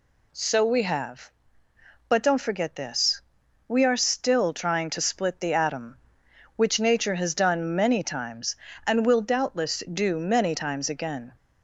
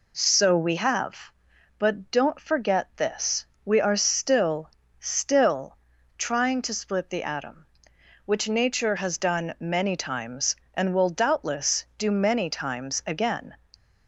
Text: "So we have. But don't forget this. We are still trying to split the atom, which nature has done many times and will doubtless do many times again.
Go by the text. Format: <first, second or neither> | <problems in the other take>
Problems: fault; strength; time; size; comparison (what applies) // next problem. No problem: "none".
first | says "still" twice; at 4.9 s